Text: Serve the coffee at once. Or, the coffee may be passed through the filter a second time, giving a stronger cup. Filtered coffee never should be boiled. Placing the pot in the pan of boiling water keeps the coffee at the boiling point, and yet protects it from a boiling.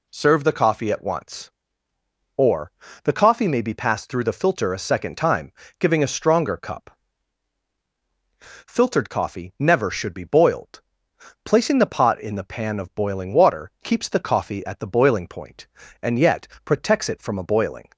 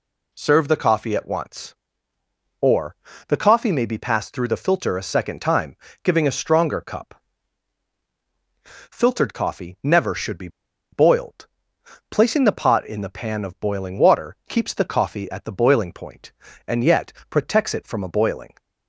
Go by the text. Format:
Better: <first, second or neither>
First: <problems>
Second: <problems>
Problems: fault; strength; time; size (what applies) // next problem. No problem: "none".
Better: first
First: pauses between "yet" and "protects"; slight; at 16.4 s; 0.18 s long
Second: pauses between "be" and "boiled"; at 10.4 s; 0.44 s long // pauses between "yet" and "protects"; slight; at 17.1 s; 0.18 s long